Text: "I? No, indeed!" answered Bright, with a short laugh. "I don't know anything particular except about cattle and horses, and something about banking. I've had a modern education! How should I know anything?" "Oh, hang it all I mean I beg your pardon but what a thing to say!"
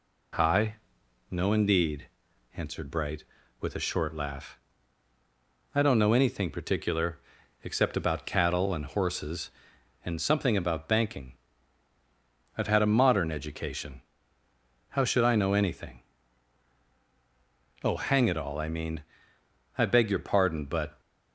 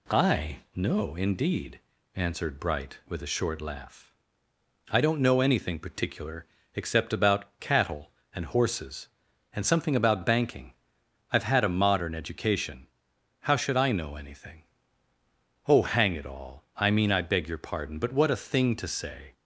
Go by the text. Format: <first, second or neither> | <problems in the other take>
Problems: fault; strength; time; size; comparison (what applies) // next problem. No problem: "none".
second | pauses between "particular" and "except"; at 7.1 s; 0.42 s long; slight in the second // pauses between "mean" and "I"; noticeable; at 19.0 s; 0.74 s long // stops before "what a thing to say"; at 20.9 s